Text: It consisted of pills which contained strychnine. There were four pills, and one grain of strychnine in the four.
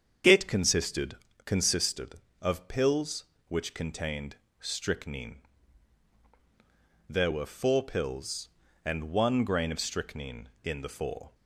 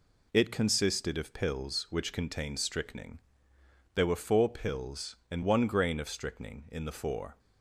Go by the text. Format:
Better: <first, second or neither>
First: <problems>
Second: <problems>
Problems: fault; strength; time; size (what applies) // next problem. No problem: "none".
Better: second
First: starts louder than the rest; strong; until 1.5 s; 8 dB // says "consisted" twice; at 1.4 s // pauses between "contained" and "strychnine"; slight; at 4.3 s; 0.22 s long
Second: none